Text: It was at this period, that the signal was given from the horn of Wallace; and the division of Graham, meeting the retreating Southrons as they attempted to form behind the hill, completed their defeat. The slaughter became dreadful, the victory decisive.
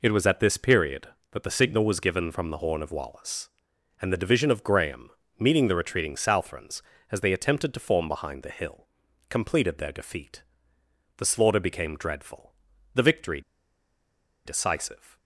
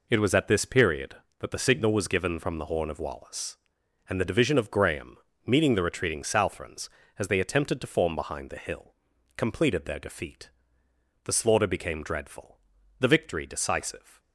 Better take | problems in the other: second | pauses between "victory" and "decisive"; at 13.4 s; 1.0 s long

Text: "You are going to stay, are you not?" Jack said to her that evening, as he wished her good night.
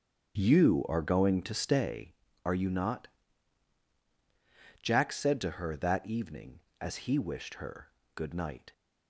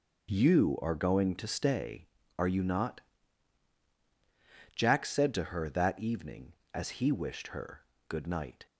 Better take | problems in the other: second | starts louder than the rest; strong; until 2.0 s; 7.5 dB // pauses between "her" and "good"; slight; at 7.9 s; 0.24 s long; slight in the second

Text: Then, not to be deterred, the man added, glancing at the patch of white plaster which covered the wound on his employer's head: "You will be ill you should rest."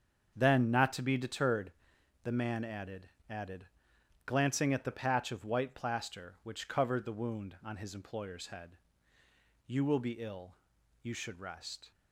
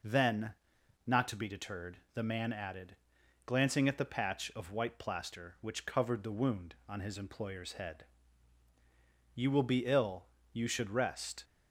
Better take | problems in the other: second | starts louder than the rest; strong; until 1.3 s; 7 dB // says "added" twice; at 3.2 s // pauses between "ill" and "you"; noticeable; at 10.5 s; 0.48 s long; slight in the second

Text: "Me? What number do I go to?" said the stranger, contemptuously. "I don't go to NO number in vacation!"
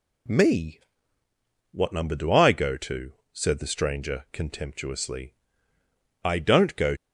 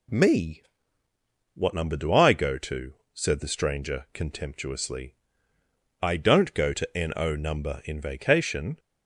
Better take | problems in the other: second | stops before "to NO number in vacation"; at 6.9 s

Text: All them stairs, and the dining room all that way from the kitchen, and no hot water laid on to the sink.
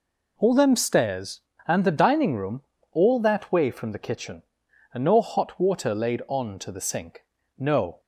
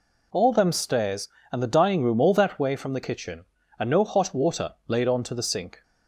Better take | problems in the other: second | pauses between "room" and "all"; slight; at 2.6 s; 0.30 s long // goes on to say "No"; slight; from 7.5 s on; 0.44 s long

